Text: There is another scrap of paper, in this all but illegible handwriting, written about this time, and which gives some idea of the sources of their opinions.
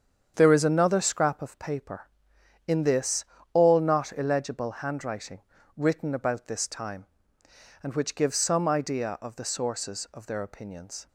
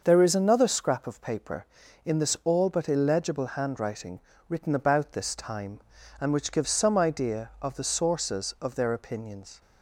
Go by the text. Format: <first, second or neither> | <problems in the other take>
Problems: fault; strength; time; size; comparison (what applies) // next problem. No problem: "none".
second | starts louder than the rest; strong; until 1.3 s; 8 dB; noticeable in the second // pauses between "this" and "all"; slight; at 3.2 s; 0.30 s long // says "not" for "but"; at 3.7 s